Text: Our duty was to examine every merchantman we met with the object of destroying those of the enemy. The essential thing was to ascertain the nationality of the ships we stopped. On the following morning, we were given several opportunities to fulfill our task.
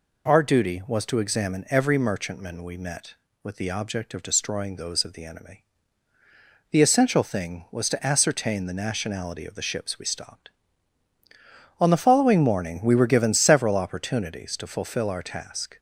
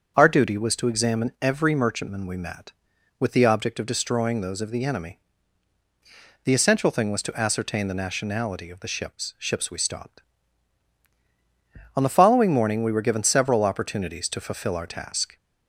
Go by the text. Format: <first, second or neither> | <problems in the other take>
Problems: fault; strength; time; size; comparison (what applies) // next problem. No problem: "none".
first | starts louder than the rest; until 1.1 s; 7 dB // says "ships" twice; at 9.3 s